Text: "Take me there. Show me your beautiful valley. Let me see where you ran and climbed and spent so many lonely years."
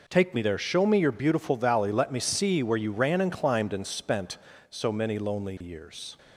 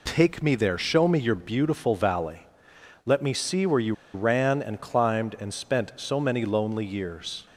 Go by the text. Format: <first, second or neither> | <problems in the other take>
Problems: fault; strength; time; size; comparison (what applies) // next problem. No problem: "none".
first | pauses between "you" and "ran"; slight; at 3.9 s; 0.21 s long